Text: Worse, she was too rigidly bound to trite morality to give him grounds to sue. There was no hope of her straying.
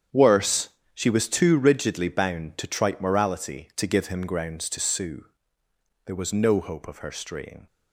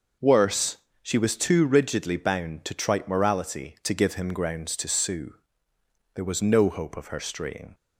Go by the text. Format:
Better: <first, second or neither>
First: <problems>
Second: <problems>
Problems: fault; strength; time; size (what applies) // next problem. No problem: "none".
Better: second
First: gets quieter; strong; throughout; 11.5 dB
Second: none